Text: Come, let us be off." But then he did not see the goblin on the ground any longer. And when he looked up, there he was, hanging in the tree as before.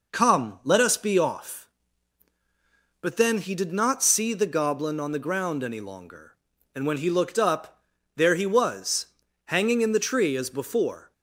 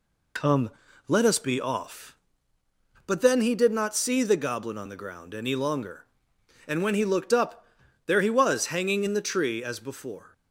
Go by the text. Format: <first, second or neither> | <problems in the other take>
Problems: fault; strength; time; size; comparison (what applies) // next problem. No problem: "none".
first | loses the start of "Come"; at 0.3 s; 45 ms